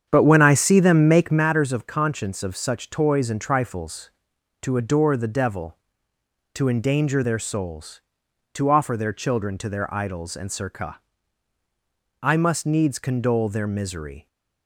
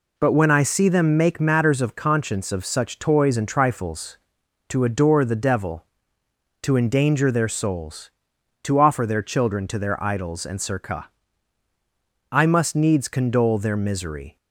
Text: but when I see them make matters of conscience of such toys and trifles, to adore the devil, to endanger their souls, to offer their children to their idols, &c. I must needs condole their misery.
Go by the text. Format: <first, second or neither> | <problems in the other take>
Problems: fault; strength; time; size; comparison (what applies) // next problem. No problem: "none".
second | starts louder than the rest; strong; until 1.5 s; 8 dB